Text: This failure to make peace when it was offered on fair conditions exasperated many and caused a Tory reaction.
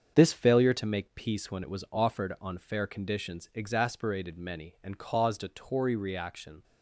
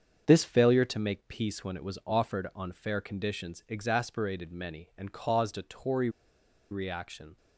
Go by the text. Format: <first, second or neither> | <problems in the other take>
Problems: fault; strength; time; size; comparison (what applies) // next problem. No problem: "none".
first | starts louder than the rest; strong; until 1.2 s; 7 dB; also in the first // pauses between "Tory" and "reaction"; noticeable; at 6.0 s; 0.61 s long